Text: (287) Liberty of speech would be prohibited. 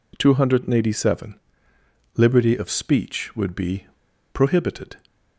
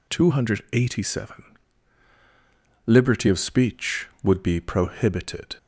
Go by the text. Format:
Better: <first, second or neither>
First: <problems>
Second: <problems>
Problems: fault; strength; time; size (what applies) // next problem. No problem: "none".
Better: second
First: pauses between "be" and "prohibited"; noticeable; at 3.8 s; 0.46 s long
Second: none